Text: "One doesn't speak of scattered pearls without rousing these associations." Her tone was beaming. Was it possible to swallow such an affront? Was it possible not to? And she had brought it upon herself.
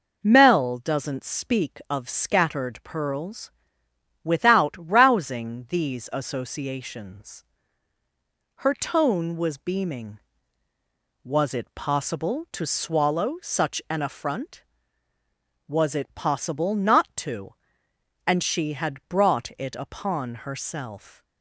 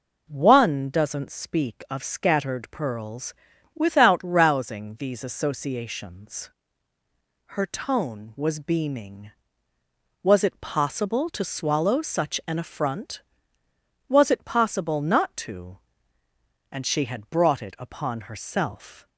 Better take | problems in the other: second | says "Mel" for "One"; at 0.2 s // pauses between "pearls" and "without"; noticeable; at 3.5 s; 0.70 s long; also in the second

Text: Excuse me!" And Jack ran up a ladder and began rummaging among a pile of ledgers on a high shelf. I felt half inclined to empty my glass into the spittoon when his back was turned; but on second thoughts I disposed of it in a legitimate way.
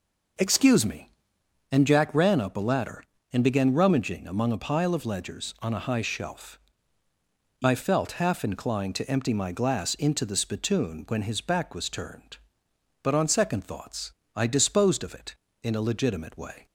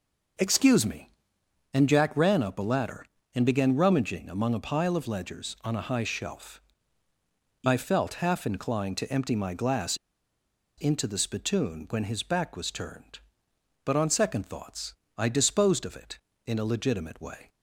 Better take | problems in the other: first | pauses between "glass" and "into"; noticeable; at 9.9 s; 0.80 s long // pauses between "thoughts" and "I"; slight; at 14.9 s; 0.24 s long; slight in the first

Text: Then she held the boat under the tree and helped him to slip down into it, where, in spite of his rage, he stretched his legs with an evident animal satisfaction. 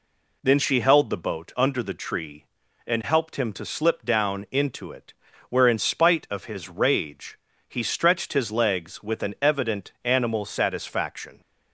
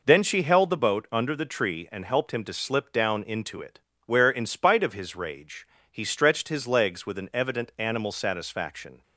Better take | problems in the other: neither | none

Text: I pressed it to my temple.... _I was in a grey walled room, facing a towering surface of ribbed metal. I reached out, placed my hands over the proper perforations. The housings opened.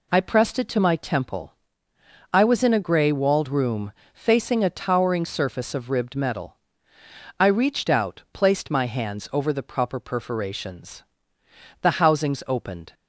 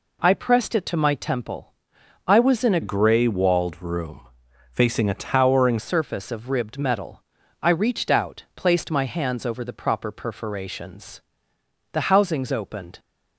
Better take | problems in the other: first | changes voice from "grey" to "towering"; from 2.8 to 5.7 s; 2.9 s long

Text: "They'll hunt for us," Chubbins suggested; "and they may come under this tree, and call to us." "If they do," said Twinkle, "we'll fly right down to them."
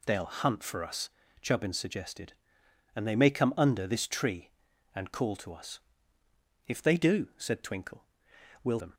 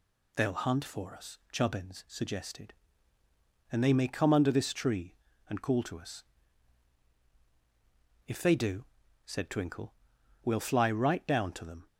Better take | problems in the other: second | skips "fly right down to"; at 8.7 s

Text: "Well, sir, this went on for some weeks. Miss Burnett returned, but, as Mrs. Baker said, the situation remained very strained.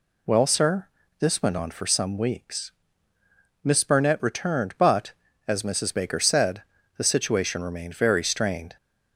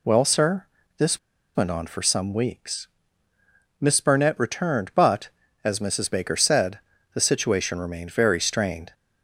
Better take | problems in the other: first | pauses between "this" and "went"; at 1.1 s; 0.38 s long

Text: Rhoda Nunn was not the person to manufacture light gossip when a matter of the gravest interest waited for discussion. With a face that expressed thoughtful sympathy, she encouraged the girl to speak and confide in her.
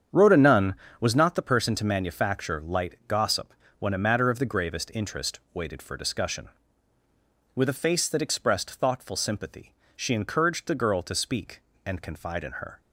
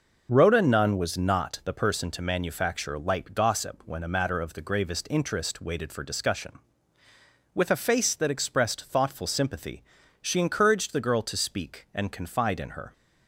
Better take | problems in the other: second | starts louder than the rest; strong; until 1.3 s; 8 dB // pauses between "gossip" and "when"; slight; at 3.5 s; 0.26 s long

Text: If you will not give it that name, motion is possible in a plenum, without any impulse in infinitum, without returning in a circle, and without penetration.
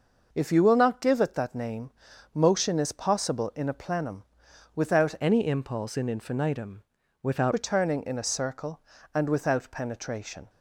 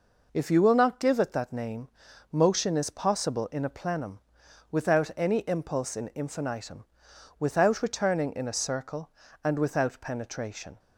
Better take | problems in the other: second | changes voice from "any" to "without"; from 5.1 to 7.5 s; 2.4 s long

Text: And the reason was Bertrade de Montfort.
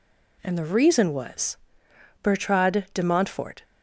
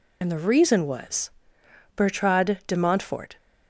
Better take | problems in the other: first | loses the start of "And"; at 0.2 s; 65 ms // pauses between "was" and "Bertrade"; noticeable; at 1.3 s; 0.66 s long; noticeable in the first

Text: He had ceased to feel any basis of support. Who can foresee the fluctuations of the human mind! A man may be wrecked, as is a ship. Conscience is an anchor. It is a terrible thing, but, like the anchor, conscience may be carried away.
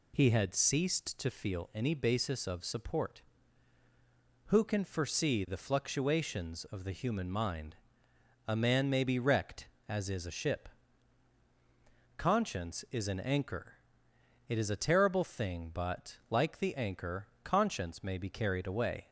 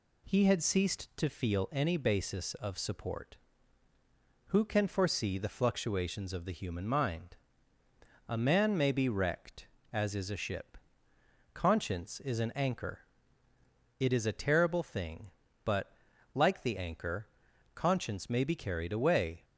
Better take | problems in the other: neither | none

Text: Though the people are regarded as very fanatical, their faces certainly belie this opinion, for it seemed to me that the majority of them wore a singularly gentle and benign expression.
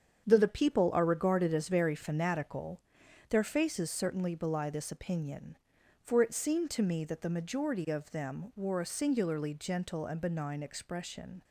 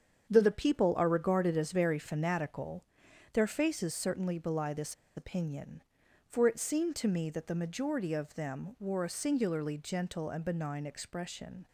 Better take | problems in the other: first | starts louder than the rest; strong; until 1.3 s; 7.5 dB; strong in the first // pauses between "this" and "opinion"; slight; at 4.9 s; 0.22 s long

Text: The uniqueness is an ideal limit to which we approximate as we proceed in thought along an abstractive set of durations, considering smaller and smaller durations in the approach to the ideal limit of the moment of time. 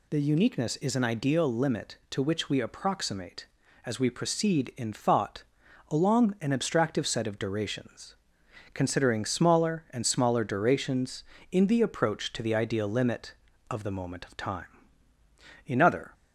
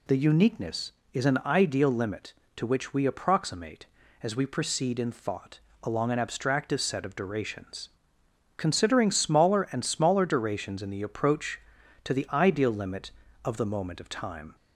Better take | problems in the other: second | pauses between "thought" and "along"; noticeable; at 5.4 s; 0.48 s long; slight in the second // goes on to say "In other"; slight; from 15.6 s on; 0.48 s long

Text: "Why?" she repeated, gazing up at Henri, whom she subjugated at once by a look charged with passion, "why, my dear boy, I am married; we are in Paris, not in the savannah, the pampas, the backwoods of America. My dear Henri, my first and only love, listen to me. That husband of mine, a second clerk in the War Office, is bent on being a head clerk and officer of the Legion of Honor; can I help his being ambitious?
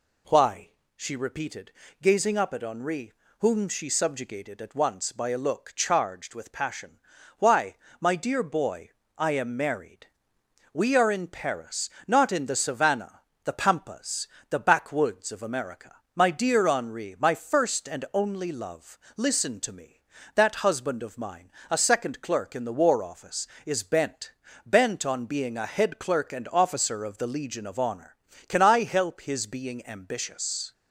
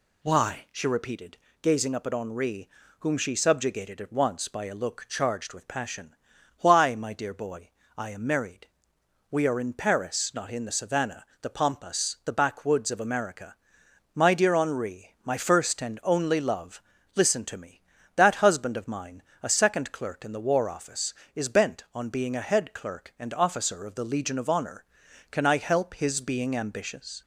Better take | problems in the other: second | says "bent" twice; at 24.6 s

